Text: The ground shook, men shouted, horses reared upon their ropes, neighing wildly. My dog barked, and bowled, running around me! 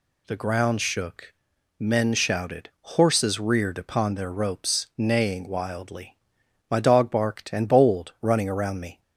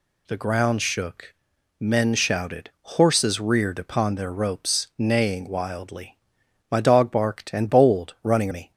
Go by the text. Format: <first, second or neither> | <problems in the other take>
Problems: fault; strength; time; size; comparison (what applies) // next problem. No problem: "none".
first | skips "around"; at 8.5 s